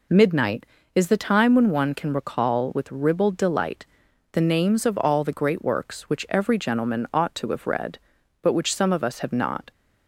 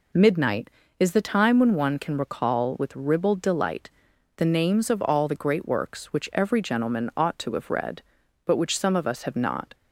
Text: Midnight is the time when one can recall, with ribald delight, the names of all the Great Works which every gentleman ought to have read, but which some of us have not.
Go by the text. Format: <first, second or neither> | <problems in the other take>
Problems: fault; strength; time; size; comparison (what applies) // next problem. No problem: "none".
neither | none